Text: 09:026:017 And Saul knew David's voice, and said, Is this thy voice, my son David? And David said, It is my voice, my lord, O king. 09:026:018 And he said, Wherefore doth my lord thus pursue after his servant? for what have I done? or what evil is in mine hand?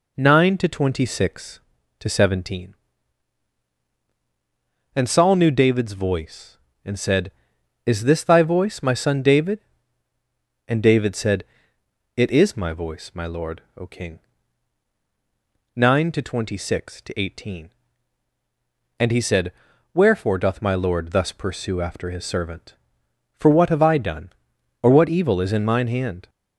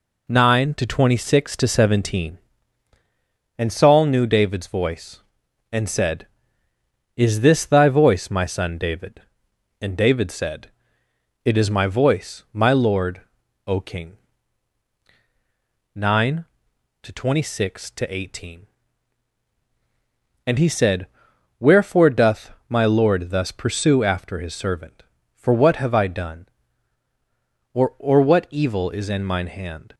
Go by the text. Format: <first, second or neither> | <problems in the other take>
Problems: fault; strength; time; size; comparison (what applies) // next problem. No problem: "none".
first | pauses between "doth" and "my"; slight; at 22.4 s; 0.18 s long // says "or" twice; at 27.9 s